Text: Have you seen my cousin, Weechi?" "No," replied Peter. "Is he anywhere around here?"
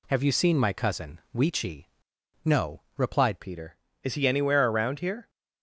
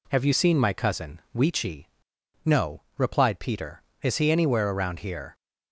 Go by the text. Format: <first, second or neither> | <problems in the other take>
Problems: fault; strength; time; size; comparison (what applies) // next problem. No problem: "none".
second | changes voice at "Peter"; from 3.3 s on; 1.9 s long